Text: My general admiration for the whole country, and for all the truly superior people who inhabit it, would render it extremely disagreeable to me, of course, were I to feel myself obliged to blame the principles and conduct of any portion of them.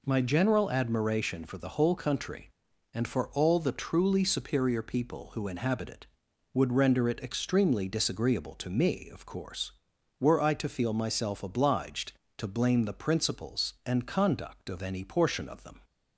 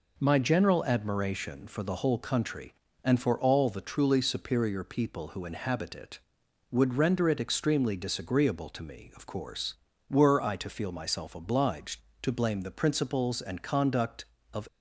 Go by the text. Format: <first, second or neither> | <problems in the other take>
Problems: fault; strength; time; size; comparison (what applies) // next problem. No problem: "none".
first | stops before "any portion of them"; at 14.6 s